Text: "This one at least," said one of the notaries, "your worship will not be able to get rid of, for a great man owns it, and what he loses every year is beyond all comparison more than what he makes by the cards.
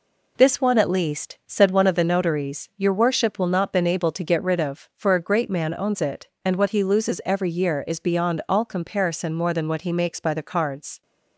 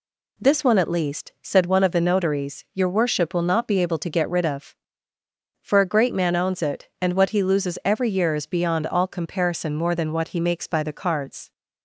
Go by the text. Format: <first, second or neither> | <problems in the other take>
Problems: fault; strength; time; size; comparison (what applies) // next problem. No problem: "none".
second | says "been" for "be"; at 3.7 s